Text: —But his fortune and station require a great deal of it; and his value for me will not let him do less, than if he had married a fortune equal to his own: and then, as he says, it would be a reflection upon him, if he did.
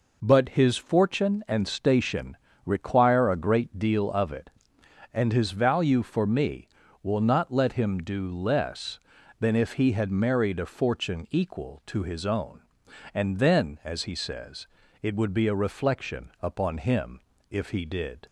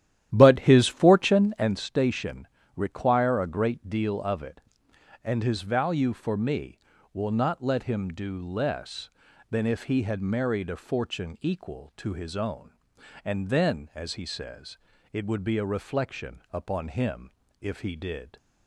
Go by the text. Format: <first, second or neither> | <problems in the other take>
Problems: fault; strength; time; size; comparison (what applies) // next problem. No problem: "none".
first | starts louder than the rest; strong; until 1.7 s; 12 dB // pauses between "station" and "require"; slight; at 2.4 s; 0.30 s long; slight in the first